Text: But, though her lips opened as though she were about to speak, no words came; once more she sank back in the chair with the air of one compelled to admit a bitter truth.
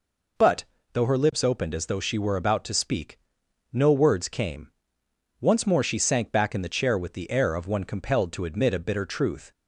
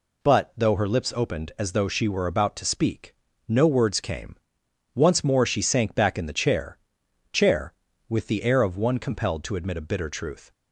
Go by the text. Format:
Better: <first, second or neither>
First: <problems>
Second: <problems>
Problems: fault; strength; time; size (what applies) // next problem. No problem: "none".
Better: first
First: none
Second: says "chair" twice; at 7.3 s